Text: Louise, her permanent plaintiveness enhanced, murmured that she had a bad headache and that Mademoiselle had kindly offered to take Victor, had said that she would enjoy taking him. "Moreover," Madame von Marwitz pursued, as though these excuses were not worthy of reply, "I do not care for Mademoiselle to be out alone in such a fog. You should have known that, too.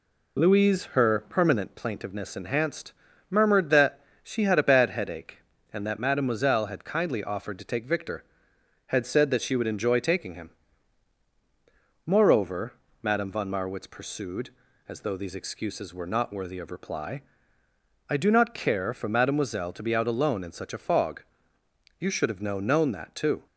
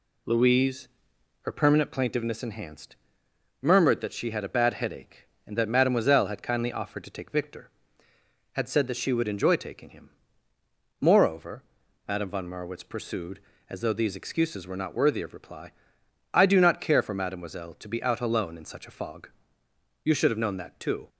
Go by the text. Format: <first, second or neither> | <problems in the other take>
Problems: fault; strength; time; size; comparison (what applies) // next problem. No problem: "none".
second | pauses between "that" and "she"; slight; at 3.9 s; 0.22 s long // says "known" twice; at 22.6 s